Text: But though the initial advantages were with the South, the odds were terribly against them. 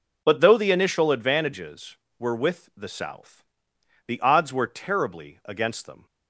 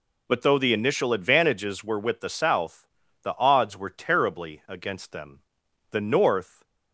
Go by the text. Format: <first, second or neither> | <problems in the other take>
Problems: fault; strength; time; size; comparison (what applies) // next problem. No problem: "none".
first | goes on to say "The North"; noticeable; from 5.9 s on; 0.72 s long